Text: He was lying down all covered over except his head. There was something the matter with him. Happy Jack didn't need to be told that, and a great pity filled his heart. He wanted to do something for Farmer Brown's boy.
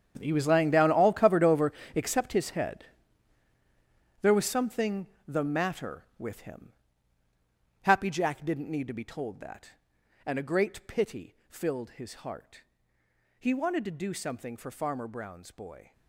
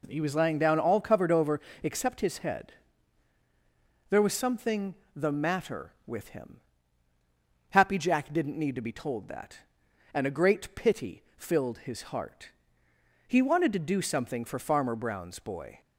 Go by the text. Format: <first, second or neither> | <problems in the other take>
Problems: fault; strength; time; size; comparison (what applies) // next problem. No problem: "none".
second | gets quieter; strong; throughout; 15.5 dB // pauses between "over" and "except"; slight; at 1.7 s; 0.22 s long; slight in the second // pauses between "something" and "the"; slight; at 5.0 s; 0.22 s long; slight in the second